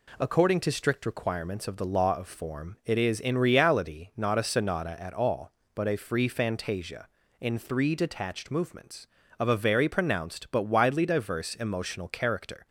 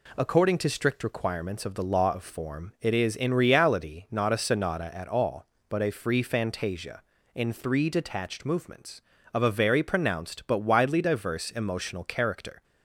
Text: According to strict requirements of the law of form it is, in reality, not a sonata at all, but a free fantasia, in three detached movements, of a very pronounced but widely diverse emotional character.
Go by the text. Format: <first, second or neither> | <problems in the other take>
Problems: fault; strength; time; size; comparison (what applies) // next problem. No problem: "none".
neither | none